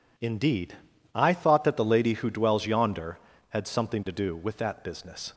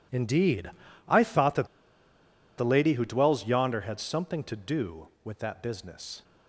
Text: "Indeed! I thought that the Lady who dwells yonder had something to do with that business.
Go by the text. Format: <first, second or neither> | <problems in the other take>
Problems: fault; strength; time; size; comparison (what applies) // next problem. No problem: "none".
first | pauses between "that" and "the"; noticeable; at 1.6 s; 0.90 s long